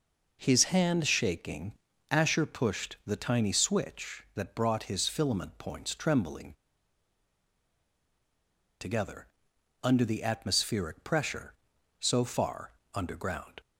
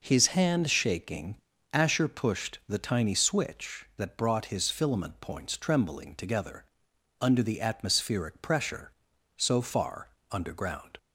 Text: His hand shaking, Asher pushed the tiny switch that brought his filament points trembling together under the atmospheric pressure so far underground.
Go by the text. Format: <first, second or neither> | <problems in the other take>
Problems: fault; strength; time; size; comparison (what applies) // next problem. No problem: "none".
second | pauses between "trembling" and "together"; strong; at 6.5 s; 2.2 s long // pauses between "together" and "under"; noticeable; at 9.2 s; 0.56 s long; noticeable in the second // pauses between "far" and "underground"; slight; at 12.7 s; 0.22 s long; slight in the second